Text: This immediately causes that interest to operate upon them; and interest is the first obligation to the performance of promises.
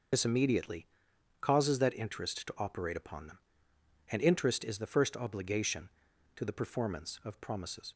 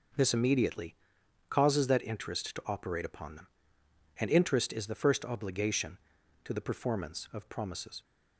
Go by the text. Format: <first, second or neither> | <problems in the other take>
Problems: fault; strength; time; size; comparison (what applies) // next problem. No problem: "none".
second | loses the start of "This"; at 0.1 s; 75 ms // pauses between "immediately" and "causes"; noticeable; at 0.8 s; 0.52 s long; noticeable in the second